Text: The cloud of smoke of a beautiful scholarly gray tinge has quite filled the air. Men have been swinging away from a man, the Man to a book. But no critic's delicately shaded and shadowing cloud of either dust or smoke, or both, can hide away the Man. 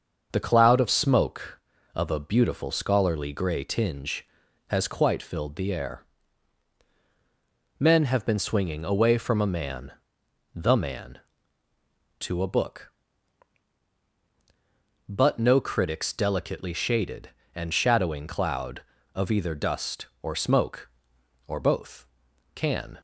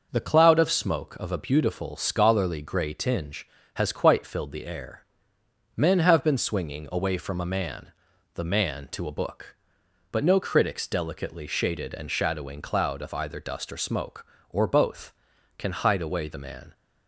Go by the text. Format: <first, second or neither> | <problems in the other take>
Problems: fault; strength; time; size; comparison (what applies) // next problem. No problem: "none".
second | starts louder than the rest; until 1.3 s; 6.5 dB // stops before "hide away the Man"; at 22.9 s